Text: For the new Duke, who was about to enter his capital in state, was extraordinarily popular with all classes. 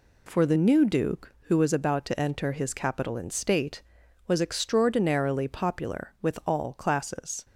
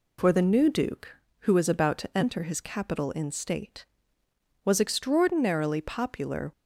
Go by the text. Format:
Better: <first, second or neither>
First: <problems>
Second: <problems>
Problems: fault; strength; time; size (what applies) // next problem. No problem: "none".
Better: first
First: none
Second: stops before "with all classes"; at 6.5 s